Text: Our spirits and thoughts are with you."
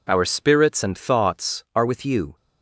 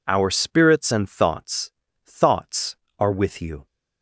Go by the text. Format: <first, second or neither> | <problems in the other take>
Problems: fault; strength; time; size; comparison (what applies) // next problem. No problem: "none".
first | says "thoughts" twice; at 2.0 s